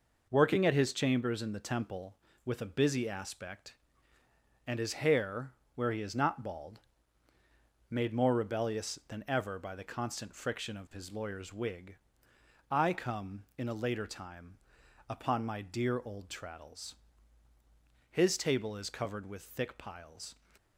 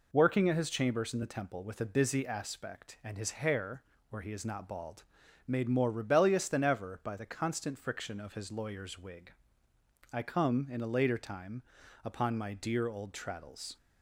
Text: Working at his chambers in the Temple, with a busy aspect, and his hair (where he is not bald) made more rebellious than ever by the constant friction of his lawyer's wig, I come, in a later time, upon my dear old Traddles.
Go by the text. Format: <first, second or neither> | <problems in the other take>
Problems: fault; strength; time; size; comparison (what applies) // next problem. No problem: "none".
second | goes on to say "His table is covered with thick piles"; strong; from 18.0 s on; 2.2 s long